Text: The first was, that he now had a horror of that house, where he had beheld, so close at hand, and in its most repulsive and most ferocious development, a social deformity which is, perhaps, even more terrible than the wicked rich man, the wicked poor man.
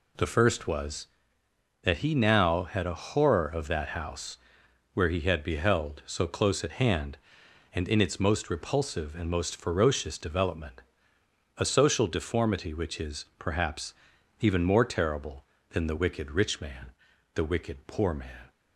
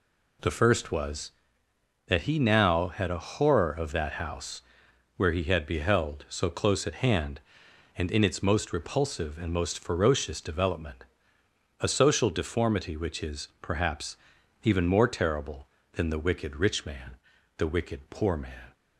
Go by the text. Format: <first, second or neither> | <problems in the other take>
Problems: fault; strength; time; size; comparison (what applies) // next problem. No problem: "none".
neither | none